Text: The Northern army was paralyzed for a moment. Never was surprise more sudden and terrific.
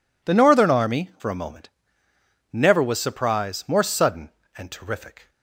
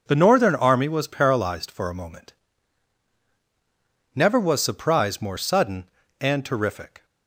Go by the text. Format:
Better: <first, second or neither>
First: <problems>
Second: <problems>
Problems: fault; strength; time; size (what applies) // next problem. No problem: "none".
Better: second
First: skips "was paralyzed"; at 1.1 s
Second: none